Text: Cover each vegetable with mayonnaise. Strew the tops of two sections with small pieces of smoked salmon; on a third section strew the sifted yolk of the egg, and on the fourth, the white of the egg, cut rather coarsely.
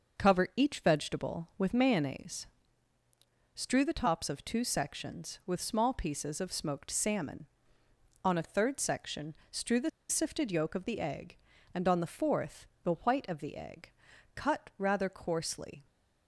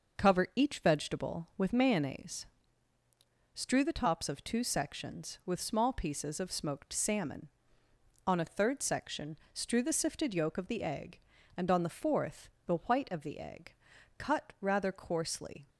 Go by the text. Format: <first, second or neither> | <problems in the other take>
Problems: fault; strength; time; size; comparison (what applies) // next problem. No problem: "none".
second | pauses between "section" and "strew"; slight; at 9.3 s; 0.16 s long; slight in the second // pauses between "the" and "sifted"; slight; at 9.8 s; 0.20 s long